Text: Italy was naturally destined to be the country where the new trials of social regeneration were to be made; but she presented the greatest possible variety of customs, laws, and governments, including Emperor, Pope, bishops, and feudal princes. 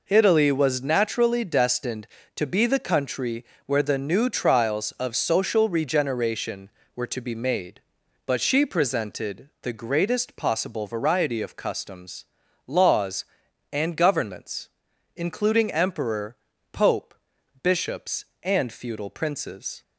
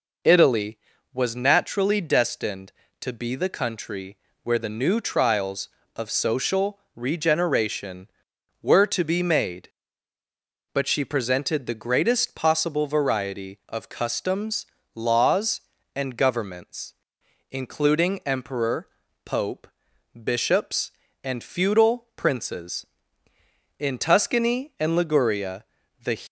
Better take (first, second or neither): first